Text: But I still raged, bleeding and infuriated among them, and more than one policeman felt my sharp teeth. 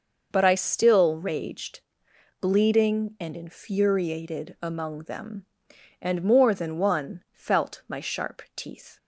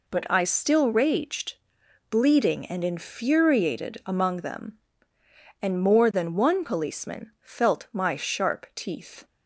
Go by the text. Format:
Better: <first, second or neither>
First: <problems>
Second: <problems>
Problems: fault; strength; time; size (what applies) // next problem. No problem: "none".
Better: second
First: skips "policeman"; at 7.2 s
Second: none